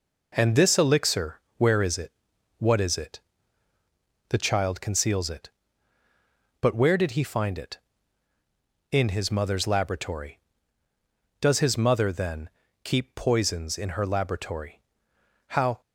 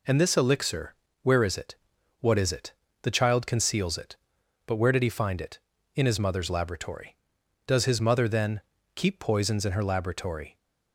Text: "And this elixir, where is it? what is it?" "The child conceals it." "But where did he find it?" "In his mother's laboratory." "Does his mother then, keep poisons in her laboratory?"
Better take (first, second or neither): second